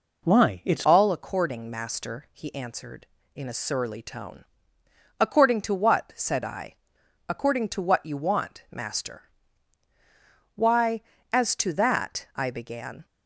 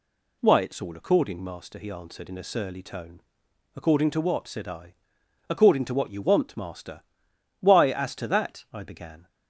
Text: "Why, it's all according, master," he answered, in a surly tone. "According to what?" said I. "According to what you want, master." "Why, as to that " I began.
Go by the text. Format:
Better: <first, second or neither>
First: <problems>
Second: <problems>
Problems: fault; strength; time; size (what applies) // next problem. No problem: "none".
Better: second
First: changes voice at "all"; from 0.8 s on; 12.2 s long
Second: none